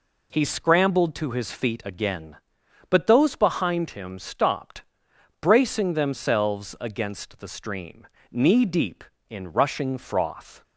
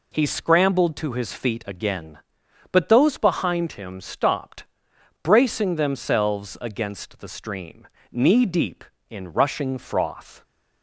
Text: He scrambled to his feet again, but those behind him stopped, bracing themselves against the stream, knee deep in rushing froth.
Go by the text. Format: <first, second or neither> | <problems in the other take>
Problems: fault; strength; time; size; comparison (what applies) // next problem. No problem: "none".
neither | none